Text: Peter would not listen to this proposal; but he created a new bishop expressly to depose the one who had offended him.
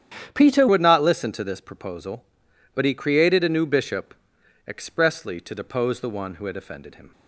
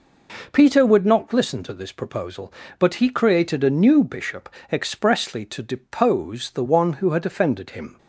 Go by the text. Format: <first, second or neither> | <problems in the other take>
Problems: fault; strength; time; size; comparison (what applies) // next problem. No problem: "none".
second | starts louder than the rest; strong; until 1.3 s; 9.5 dB // changes voice at "would"; from 0.6 s on; 6.5 s long // pauses between "bishop" and "expressly"; noticeable; at 4.1 s; 0.54 s long; slight in the second